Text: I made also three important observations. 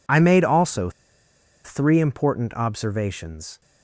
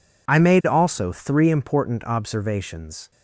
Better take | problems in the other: second | pauses between "also" and "three"; noticeable; at 0.9 s; 0.74 s long

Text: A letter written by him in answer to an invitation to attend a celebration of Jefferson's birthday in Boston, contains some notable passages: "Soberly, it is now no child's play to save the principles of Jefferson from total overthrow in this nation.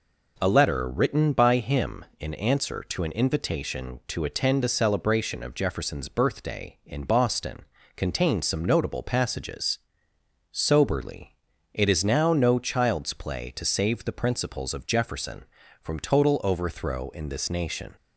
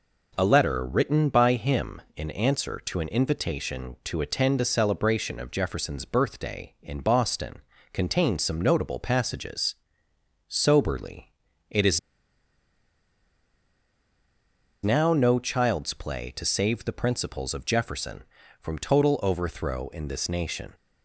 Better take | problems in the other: first | pauses between "is" and "now"; strong; at 11.9 s; 2.8 s long

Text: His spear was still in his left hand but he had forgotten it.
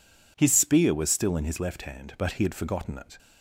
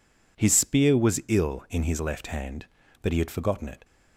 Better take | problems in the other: first | says "ill" for "still"; at 1.2 s

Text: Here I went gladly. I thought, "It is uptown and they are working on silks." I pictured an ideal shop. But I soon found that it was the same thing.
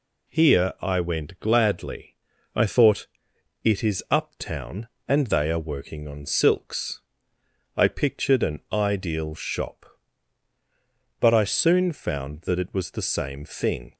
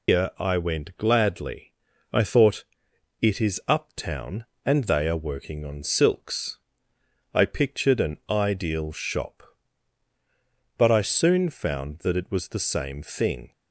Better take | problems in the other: first | loses the start of "Here"; at 0.0 s; 230 ms

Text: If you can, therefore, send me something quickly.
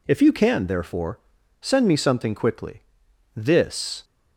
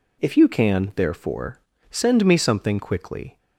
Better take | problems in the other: second | goes on to say "This"; noticeable; from 3.3 s on; 0.68 s long

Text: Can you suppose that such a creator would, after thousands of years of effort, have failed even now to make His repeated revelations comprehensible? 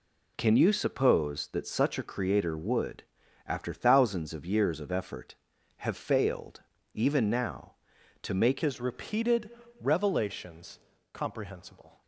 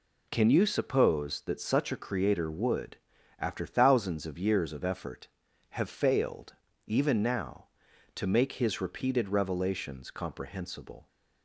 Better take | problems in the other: second | pauses between "failed" and "even"; slight; at 6.6 s; 0.32 s long; slight in the second // changes voice at "His"; from 8.6 s on; 3.4 s long // pauses between "repeated" and "revelations"; slight; at 9.4 s; 0.30 s long // pauses between "revelations" and "comprehensible"; slight; at 10.7 s; 0.36 s long

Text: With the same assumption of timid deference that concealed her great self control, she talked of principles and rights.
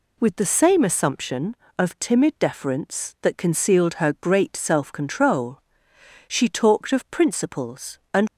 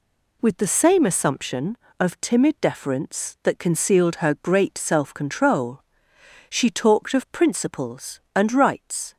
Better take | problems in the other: second | stops before "rights"; at 8.2 s

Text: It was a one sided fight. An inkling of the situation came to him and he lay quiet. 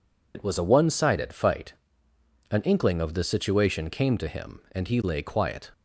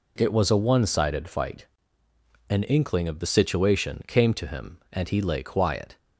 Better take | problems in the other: second | loses the start of "It"; at 0.3 s; 70 ms

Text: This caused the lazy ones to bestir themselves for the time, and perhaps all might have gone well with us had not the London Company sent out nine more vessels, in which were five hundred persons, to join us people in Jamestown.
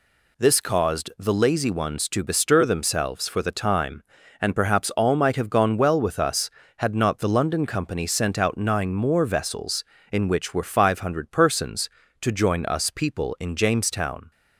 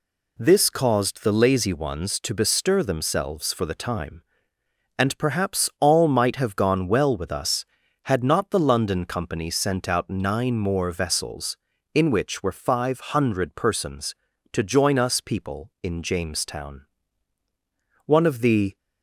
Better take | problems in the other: first | goes on to say "One of the"; noticeable; from 18.0 s on; 0.72 s long

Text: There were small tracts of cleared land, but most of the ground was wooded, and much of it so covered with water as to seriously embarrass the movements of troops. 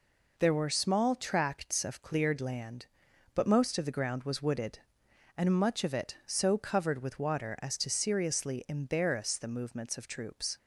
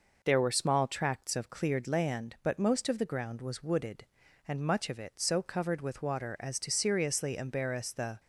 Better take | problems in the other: first | stops before "movements of troops"; at 8.1 s

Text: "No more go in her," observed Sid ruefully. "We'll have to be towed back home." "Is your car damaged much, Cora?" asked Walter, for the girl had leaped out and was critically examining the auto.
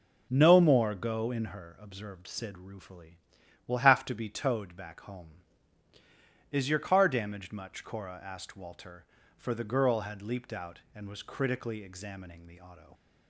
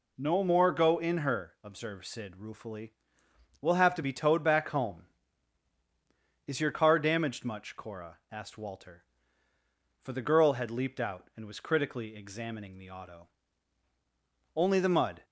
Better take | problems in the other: first | goes on to say "Only the mud"; noticeable; from 14.5 s on; 0.70 s long

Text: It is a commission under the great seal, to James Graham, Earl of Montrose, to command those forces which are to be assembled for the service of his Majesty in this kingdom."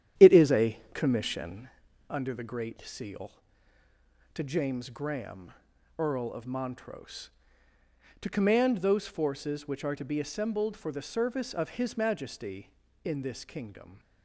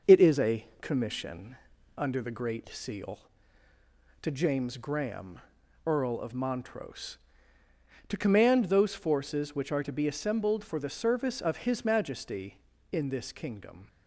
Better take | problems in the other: second | starts louder than the rest; strong; until 1.7 s; 10.5 dB // pauses between "a" and "commission"; slight; at 0.7 s; 0.16 s long; slight in the second // pauses between "commission" and "under"; at 1.6 s; 0.42 s long; also in the second

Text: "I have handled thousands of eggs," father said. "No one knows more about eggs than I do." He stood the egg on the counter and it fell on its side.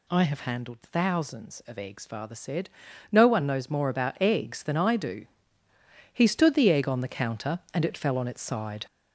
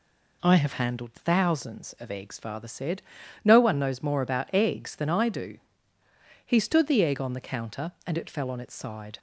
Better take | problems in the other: second | gets louder; noticeable; throughout; 5.5 dB

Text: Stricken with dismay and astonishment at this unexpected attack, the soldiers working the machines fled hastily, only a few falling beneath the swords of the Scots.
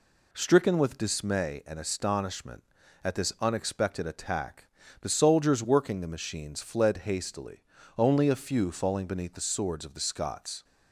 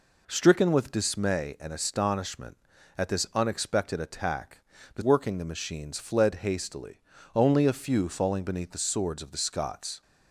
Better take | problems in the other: first | skips "soldiers"; at 5.0 s

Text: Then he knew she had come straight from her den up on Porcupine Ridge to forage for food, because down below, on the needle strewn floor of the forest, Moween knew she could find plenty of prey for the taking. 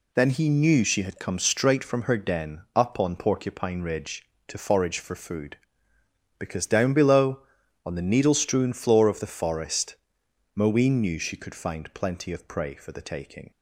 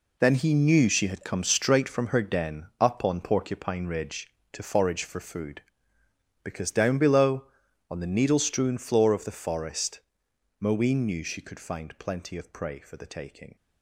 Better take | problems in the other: first | gets quieter; strong; throughout; 11 dB

